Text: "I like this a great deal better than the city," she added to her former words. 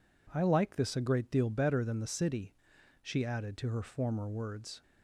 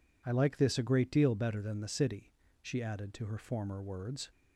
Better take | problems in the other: neither | none

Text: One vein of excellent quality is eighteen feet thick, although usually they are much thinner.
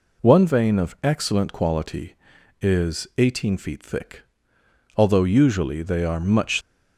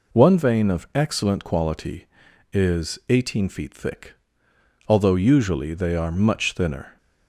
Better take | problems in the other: second | stops before "thinner"; at 6.6 s

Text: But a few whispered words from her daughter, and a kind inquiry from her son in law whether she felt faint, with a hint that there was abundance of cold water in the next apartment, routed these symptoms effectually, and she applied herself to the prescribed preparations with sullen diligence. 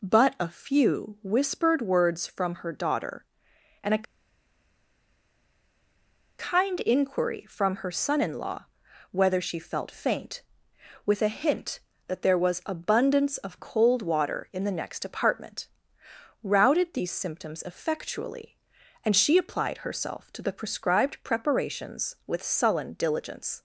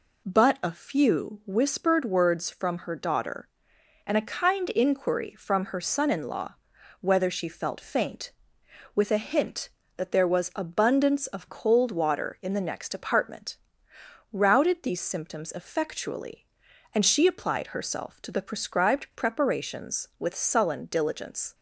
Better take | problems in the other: second | pauses between "a" and "kind"; strong; at 4.0 s; 2.3 s long // pauses between "law" and "whether"; noticeable; at 8.6 s; 0.46 s long; noticeable in the second

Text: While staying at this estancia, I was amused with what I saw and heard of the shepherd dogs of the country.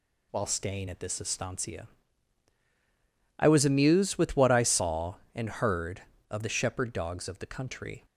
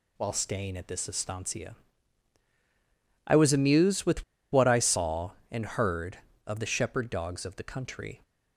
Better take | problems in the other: first | pauses between "with" and "what"; slight; at 4.2 s; 0.28 s long

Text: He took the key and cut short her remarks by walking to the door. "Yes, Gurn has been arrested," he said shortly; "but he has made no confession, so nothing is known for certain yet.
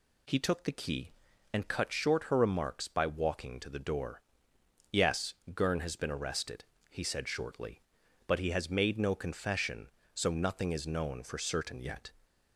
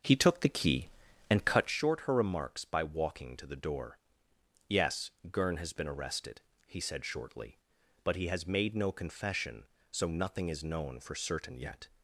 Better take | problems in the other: first | starts louder than the rest; noticeable; until 1.8 s; 6 dB

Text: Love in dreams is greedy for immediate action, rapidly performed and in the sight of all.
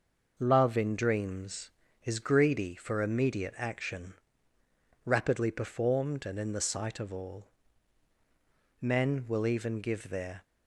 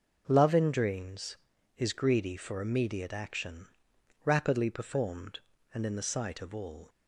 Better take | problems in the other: second | goes on to say "Men will even give their"; from 8.7 s on; 1.6 s long

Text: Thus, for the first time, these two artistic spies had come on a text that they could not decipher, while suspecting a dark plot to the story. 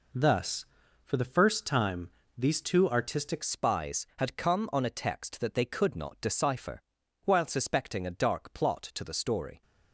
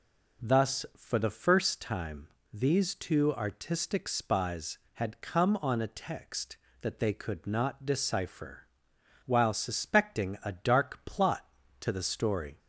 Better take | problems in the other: second | changes voice at "spies"; from 3.4 s on; 6.2 s long

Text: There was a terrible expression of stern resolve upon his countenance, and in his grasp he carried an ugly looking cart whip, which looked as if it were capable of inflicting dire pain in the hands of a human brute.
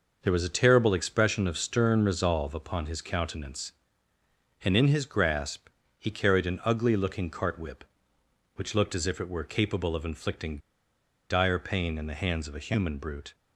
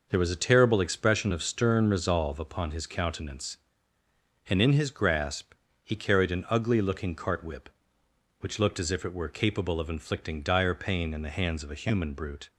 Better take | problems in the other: second | pauses between "grasp" and "he"; slight; at 5.6 s; 0.30 s long; slight in the second // pauses between "inflicting" and "dire"; noticeable; at 10.5 s; 0.70 s long

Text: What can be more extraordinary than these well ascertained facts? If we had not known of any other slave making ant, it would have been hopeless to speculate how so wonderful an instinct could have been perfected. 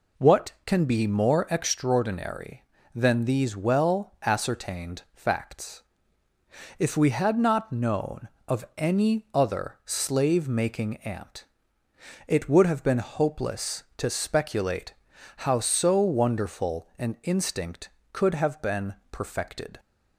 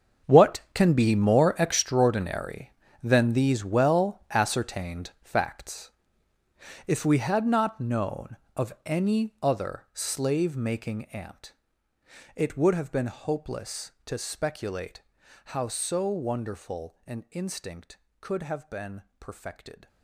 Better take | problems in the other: first | gets quieter; strong; throughout; 14.5 dB // pauses between "speculate" and "how"; at 15.0 s; 0.44 s long; also in the first // pauses between "been" and "perfected"; slight; at 19.0 s; 0.18 s long; slight in the first

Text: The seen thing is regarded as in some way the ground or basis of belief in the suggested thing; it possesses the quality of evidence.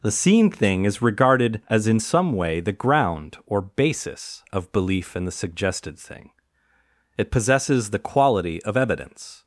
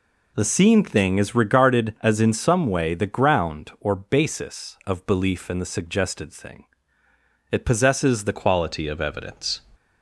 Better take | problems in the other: first | changes voice at "quality"; from 8.3 s on; 1.3 s long

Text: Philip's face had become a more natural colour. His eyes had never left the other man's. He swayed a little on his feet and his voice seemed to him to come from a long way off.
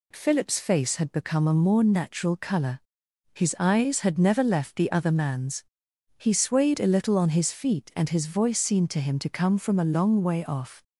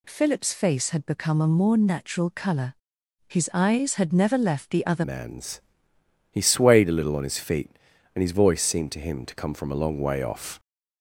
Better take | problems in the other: first | changes voice at "man's"; from 5.0 s on; 5.5 s long

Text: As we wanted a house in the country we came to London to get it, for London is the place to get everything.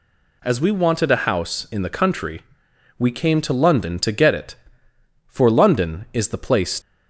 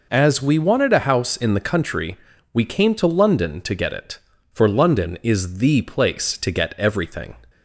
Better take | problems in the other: second | pauses between "country" and "we"; noticeable; at 2.4 s; 0.58 s long; slight in the second // stops before "to get everything"; at 6.8 s

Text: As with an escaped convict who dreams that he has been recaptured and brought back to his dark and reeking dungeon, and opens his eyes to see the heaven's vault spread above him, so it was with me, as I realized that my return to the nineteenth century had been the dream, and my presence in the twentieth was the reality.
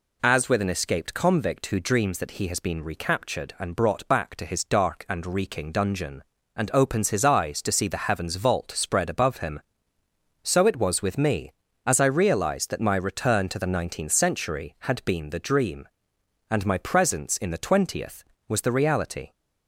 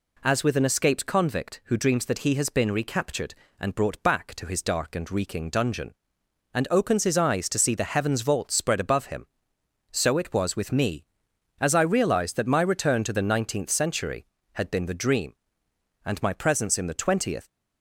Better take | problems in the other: first | stops before "was the reality"; at 17.4 s

